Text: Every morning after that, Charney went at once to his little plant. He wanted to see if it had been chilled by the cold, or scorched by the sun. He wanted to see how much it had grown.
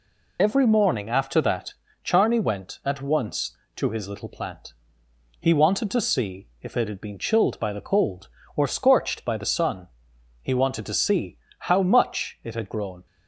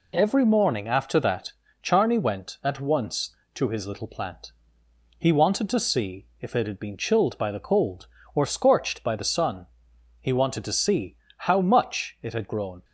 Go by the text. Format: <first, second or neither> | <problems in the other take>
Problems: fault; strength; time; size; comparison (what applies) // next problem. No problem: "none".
second | loses the start of "Every"; at 0.3 s; 55 ms // pauses between "see" and "how"; slight; at 11.3 s; 0.22 s long; slight in the second